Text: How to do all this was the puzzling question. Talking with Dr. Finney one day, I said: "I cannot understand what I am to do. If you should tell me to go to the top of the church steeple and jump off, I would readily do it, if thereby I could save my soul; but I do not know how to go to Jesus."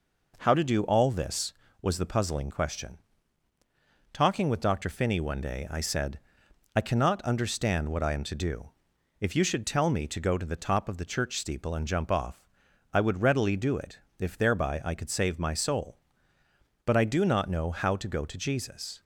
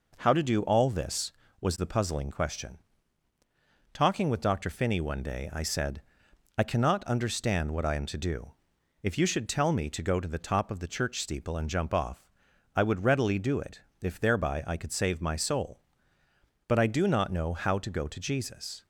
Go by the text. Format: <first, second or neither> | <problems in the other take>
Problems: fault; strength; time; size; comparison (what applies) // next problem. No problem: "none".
neither | none